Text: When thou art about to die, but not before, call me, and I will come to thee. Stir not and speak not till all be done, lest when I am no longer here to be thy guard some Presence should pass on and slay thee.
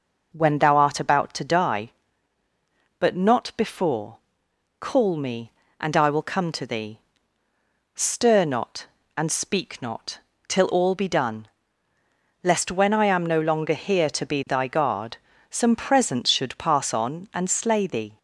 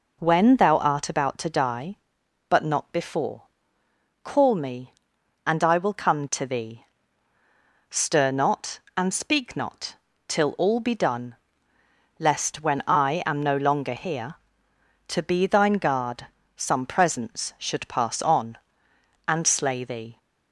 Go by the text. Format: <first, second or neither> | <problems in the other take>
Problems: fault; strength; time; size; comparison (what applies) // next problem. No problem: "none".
first | pauses between "not" and "till"; slight; at 9.9 s; 0.32 s long; slight in the first // says "thine" for "thy"; at 15.4 s // pauses between "guard" and "some"; slight; at 16.2 s; 0.30 s long; slight in the first